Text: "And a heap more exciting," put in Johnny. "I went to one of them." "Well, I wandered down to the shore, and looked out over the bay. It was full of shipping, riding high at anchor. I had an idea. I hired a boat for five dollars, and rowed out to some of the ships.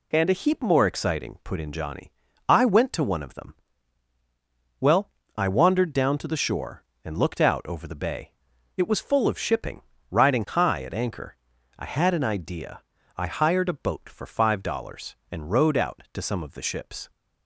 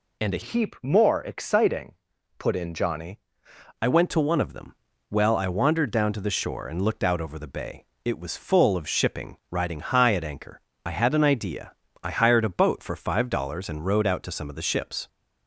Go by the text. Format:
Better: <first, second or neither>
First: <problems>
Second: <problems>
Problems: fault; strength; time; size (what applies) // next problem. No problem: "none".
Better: first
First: none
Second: changes voice from "heap" to "Johnny"; from 0.4 to 3.1 s; 2.7 s long